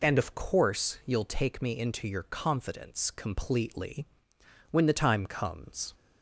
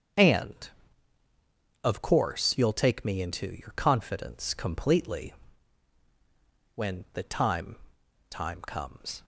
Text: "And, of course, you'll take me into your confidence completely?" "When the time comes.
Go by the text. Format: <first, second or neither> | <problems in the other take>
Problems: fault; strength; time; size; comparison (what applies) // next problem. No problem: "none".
first | starts louder than the rest; strong; until 2.2 s; 7.5 dB // says "time" twice; at 8.2 s